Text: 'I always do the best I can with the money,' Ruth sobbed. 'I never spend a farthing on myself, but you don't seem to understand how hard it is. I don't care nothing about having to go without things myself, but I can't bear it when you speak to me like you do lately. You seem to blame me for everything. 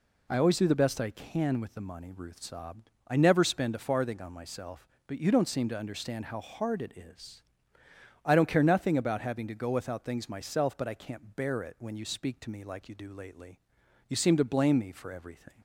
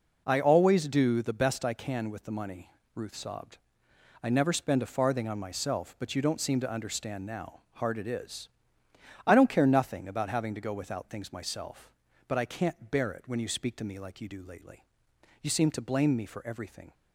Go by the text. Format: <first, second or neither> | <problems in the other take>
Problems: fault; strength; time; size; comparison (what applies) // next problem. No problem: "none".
first | says "now" for "how"; at 7.2 s